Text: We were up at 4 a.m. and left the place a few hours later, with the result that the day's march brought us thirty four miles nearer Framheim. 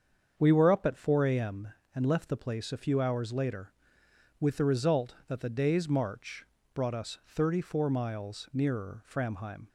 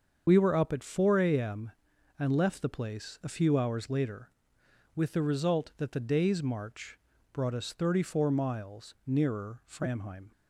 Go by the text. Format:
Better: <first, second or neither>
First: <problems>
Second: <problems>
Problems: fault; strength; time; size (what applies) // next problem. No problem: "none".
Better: first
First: starts louder than the rest; strong; until 1.3 s; 7 dB // pauses between "march" and "brought"; slight; at 6.4 s; 0.30 s long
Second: loses the start of "We"; at 0.2 s; 70 ms // starts louder than the rest; until 1.2 s; 7 dB // pauses between "march" and "brought"; slight; at 6.9 s; 0.34 s long